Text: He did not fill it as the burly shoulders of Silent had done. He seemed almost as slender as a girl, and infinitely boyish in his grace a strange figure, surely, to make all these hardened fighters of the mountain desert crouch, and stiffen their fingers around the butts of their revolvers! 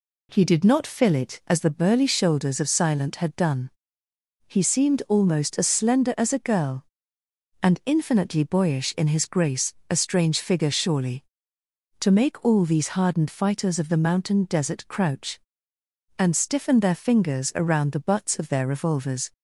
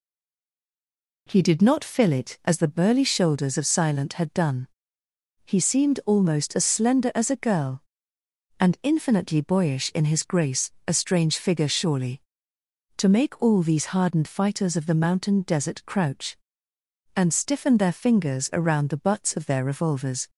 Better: first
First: pauses between "grace" and "a"; slight; at 9.7 s; 0.16 s long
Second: stays silent before the first word; noticeable; until 1.2 s; 1.2 s long // pauses between "grace" and "a"; slight; at 10.7 s; 0.16 s long

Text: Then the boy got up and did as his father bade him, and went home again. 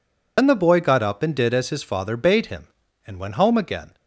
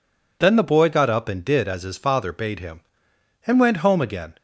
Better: second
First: loses the start of "Then"; at 0.3 s; 70 ms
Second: none

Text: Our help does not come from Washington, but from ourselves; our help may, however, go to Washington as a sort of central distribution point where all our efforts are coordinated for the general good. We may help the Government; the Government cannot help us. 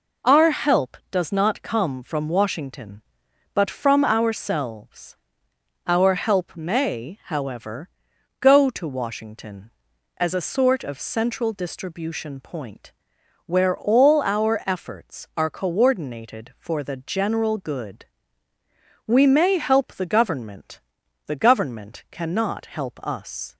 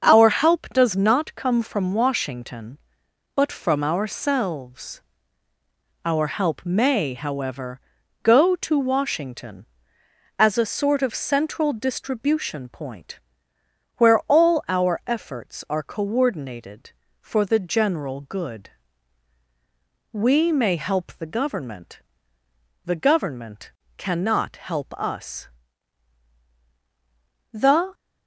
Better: first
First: pauses between "point" and "where"; noticeable; at 12.9 s; 0.54 s long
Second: starts louder than the rest; until 1.1 s; 6.5 dB // pauses between "point" and "where"; noticeable; at 13.1 s; 0.78 s long // pauses between "Government" and "cannot"; slight; at 23.7 s; 0.16 s long // goes on to say "The"; slight; from 27.5 s on; 0.40 s long

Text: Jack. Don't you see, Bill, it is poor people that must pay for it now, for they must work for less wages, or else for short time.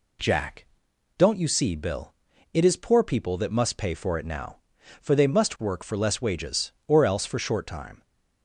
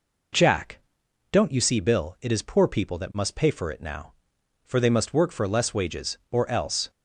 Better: first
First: none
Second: stops before "for short time"; at 6.8 s

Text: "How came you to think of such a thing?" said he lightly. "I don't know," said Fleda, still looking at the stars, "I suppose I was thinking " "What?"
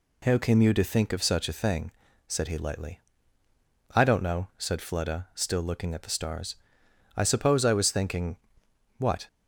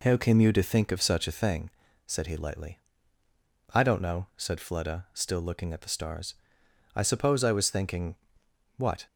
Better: first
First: none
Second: starts louder than the rest; noticeable; until 1.6 s; 4 dB

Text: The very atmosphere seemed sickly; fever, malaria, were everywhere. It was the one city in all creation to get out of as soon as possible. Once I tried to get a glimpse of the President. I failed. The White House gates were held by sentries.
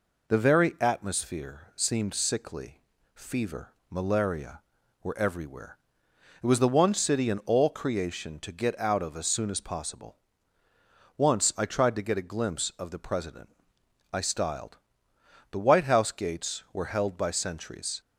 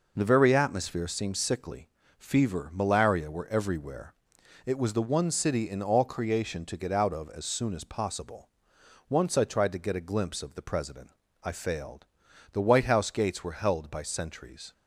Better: second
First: says "styled" for "failed"; at 14.2 s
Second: none

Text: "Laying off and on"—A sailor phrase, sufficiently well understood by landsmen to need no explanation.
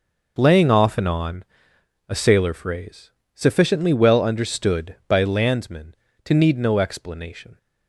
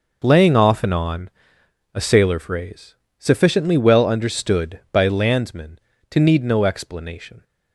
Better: neither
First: none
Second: none

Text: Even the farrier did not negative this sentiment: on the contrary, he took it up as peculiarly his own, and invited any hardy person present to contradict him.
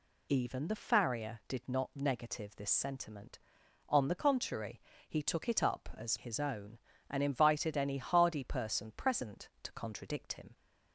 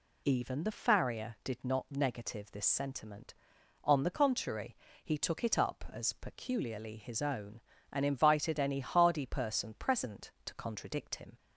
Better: second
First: skips "peculiarly"; at 6.1 s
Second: none

